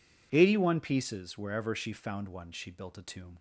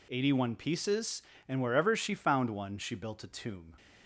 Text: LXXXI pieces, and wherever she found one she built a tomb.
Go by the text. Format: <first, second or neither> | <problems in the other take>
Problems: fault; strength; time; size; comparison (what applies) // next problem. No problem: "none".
second | skips "and"; at 1.3 s